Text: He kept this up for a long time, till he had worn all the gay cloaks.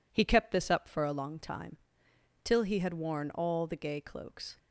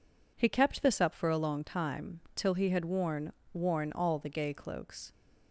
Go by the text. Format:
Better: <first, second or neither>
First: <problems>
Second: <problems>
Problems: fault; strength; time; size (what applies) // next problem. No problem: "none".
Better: first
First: none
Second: says "worn" twice; at 3.5 s